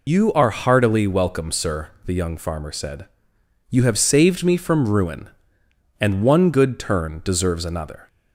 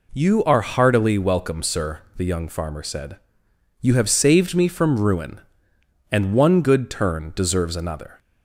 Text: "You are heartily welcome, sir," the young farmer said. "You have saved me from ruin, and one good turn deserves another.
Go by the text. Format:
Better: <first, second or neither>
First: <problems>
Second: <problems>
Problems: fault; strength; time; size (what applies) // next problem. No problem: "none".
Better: second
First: loses the start of "You"; at 0.0 s; 90 ms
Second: none